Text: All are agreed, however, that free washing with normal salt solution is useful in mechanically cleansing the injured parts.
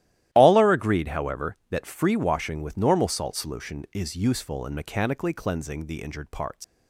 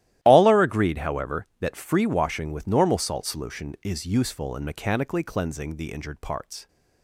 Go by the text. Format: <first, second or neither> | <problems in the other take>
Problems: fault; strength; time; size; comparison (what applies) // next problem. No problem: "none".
second | starts louder than the rest; strong; until 1.3 s; 14 dB; strong in the second // leaves "parts" unfinished; at 6.6 s; 130 ms